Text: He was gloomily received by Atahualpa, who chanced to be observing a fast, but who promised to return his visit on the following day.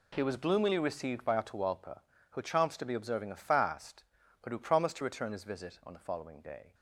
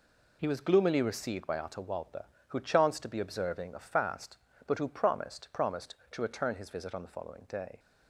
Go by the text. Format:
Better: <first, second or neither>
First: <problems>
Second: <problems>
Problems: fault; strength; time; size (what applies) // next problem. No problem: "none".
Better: first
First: none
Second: says "promised" twice; at 5.5 s